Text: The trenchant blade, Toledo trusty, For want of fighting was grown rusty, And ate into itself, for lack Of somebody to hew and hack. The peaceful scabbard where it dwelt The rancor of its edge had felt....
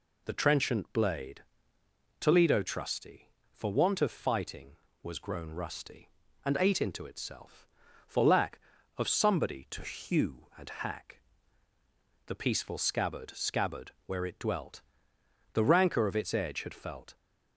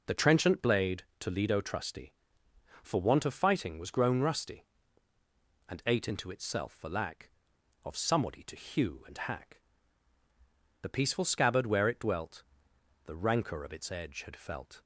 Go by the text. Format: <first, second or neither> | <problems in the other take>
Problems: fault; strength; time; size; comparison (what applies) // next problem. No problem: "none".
second | says "scabbard" twice; at 13.3 s // pauses between "dwelt" and "The"; noticeable; at 14.8 s; 0.72 s long; noticeable in the second